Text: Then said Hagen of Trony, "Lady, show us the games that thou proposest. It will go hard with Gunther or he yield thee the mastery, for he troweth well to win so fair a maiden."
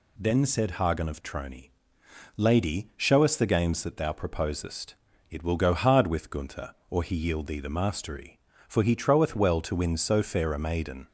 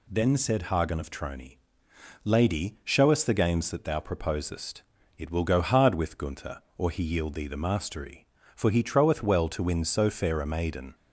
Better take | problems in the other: neither | none

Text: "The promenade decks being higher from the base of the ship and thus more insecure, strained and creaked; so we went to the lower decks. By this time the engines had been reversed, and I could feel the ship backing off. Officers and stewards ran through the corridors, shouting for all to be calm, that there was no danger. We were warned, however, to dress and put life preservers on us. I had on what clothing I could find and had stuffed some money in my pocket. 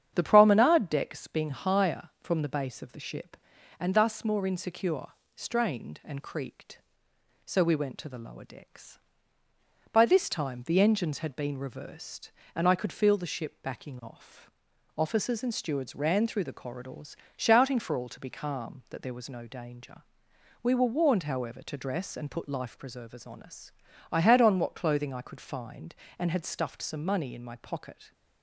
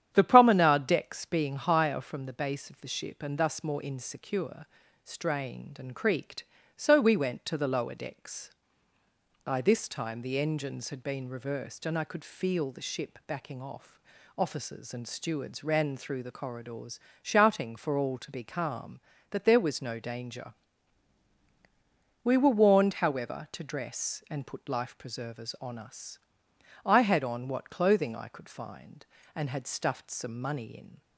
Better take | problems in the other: first | starts louder than the rest; strong; until 1.1 s; 10 dB; strong in the first // stops before "my pocket"; at 31.0 s

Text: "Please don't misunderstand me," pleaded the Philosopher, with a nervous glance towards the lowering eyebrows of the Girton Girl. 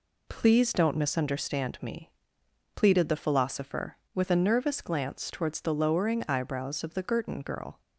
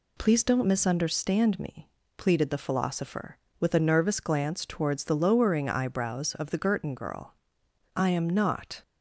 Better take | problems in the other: first | goes on to say "I am not"; noticeable; from 7.9 s on; 0.86 s long

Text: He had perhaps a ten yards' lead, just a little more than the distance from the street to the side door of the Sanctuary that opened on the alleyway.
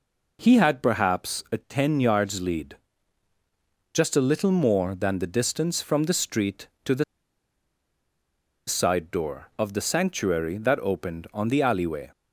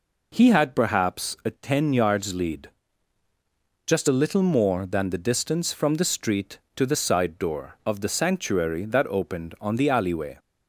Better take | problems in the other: second | pauses between "the" and "side"; strong; at 7.0 s; 1.6 s long

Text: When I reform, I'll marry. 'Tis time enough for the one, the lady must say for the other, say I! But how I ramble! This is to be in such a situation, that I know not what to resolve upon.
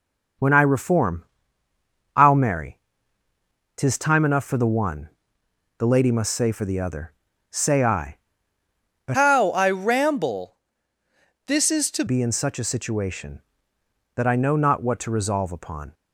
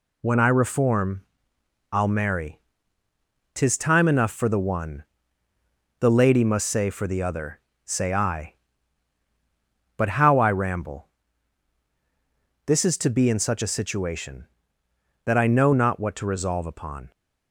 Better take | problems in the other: second | changes voice from "how" to "to"; from 9.1 to 12.0 s; 2.9 s long

